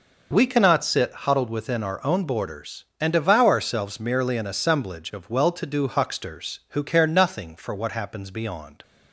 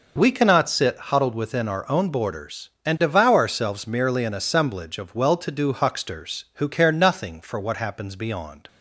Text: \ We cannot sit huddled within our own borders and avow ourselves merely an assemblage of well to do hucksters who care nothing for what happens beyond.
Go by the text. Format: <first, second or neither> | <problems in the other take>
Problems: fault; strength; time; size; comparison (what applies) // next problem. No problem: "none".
neither | none